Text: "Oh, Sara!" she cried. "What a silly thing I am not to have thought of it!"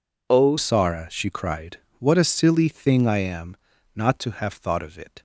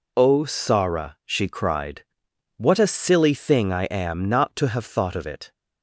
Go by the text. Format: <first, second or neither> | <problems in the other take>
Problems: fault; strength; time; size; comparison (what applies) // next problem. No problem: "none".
second | changes voice at "Sara"; from 0.5 s on; 4.7 s long // pauses between "am" and "not"; at 3.5 s; 0.40 s long